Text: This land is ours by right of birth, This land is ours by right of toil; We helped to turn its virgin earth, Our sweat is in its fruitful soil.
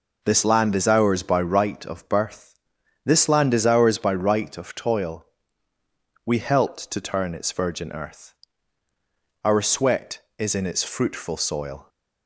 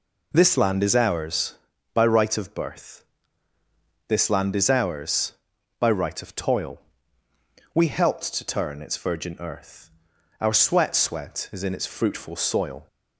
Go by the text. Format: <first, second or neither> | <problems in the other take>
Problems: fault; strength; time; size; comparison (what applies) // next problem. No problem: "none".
first | says "sweat" twice; at 10.9 s